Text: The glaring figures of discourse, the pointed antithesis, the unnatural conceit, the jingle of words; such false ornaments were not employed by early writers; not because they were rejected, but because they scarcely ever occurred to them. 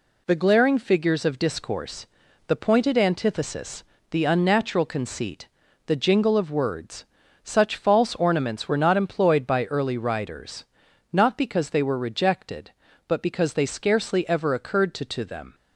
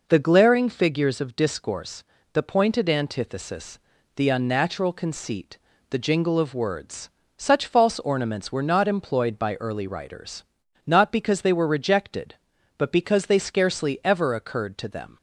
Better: second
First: says "to" twice; at 15.0 s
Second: none

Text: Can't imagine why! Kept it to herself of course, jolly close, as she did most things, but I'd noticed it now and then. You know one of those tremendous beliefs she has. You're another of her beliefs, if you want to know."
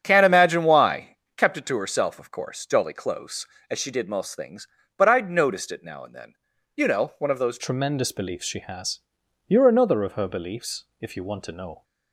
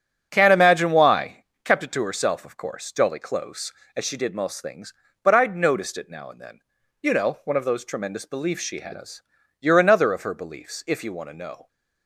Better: second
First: starts louder than the rest; strong; until 1.0 s; 8.5 dB // changes voice at "tremendous"; from 7.5 s on; 4.3 s long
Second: starts louder than the rest; strong; until 1.3 s; 7.5 dB

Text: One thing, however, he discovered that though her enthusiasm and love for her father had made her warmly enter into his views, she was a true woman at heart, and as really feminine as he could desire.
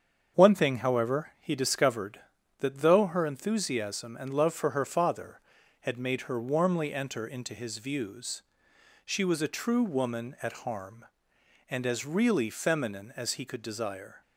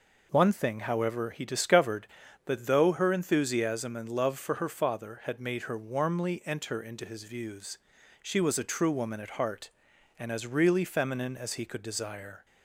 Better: second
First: starts louder than the rest; strong; until 1.4 s; 7.5 dB // says "harm" for "heart"; at 10.5 s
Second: none

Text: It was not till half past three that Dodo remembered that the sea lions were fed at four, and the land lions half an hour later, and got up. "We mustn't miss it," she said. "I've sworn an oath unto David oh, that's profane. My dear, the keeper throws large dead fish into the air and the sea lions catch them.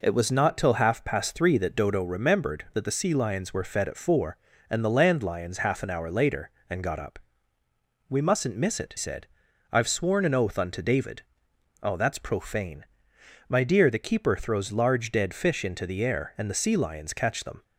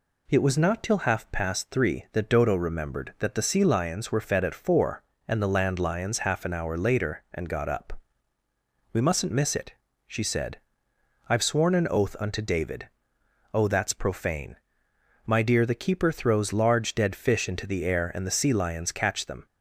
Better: second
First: skips "she"; at 8.9 s // pauses between "David" and "oh"; noticeable; at 11.2 s; 0.58 s long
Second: pauses between "David" and "oh"; noticeable; at 12.8 s; 0.66 s long

